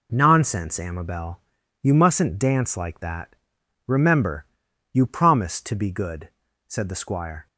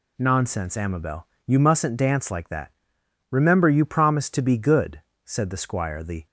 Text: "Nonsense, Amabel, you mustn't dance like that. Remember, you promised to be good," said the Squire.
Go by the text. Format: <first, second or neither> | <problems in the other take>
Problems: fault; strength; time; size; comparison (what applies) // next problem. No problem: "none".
first | goes on to say "The"; slight; from 6.0 s on; 0.24 s long